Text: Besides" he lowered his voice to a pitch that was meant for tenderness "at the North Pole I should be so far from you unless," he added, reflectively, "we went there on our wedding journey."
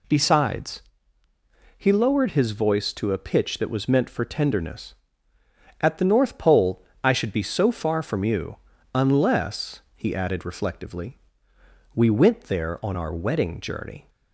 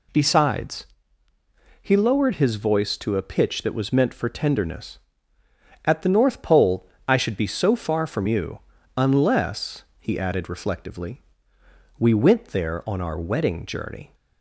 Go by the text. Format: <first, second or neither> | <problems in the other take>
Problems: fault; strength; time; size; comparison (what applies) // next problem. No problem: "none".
neither | pauses between "Besides" and "he"; noticeable; the same in both // pauses between "Pole" and "I"; slight; the same in both // pauses between "you" and "unless"; slight; the same in both